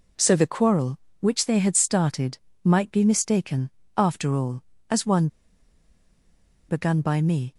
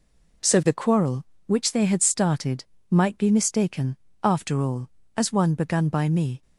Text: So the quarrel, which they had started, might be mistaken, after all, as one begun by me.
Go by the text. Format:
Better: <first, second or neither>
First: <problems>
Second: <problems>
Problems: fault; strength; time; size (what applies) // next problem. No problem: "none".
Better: second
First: pauses between "one" and "begun"; strong; at 5.2 s; 1.4 s long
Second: none